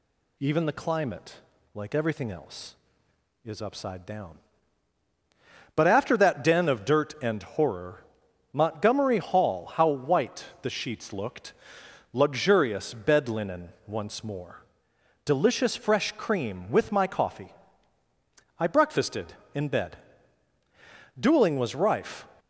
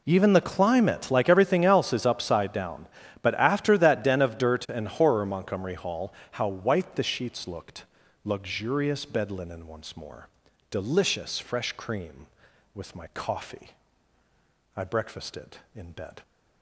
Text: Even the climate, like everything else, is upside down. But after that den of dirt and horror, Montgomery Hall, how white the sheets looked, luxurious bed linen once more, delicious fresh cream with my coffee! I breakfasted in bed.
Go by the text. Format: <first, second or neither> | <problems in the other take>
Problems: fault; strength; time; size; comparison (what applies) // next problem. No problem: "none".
second | pauses between "white" and "the"; slight; at 10.4 s; 0.16 s long // pauses between "linen" and "once"; slight; at 13.6 s; 0.16 s long // goes on to say "Dueling was rife"; noticeable; from 21.1 s on; 1.0 s long